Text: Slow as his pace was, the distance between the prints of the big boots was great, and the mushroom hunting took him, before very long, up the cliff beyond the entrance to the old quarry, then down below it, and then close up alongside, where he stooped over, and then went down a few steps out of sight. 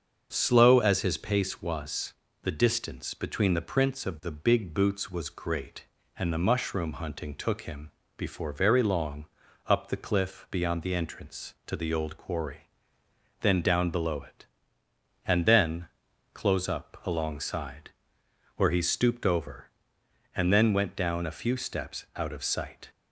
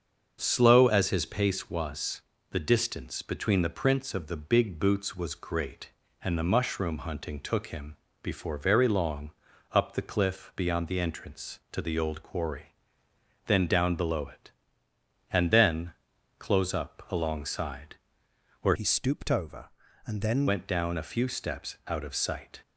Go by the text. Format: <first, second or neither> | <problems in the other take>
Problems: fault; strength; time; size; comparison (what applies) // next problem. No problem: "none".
first | starts louder than the rest; until 1.4 s; 7 dB; also in the first // pauses between "then" and "close"; noticeable; at 15.9 s; 0.46 s long; noticeable in the first // changes voice from "he" to "then"; from 18.7 to 20.4 s; 1.7 s long